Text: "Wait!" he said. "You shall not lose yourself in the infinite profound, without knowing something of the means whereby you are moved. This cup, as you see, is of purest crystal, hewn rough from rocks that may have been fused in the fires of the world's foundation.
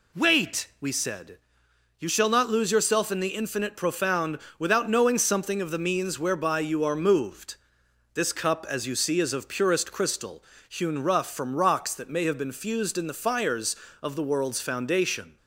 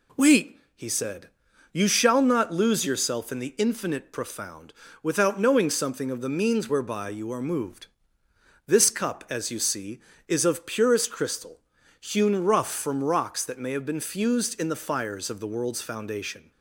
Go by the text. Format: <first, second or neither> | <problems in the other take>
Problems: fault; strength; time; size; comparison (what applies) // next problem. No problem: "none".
second | says "we" for "he"; at 0.8 s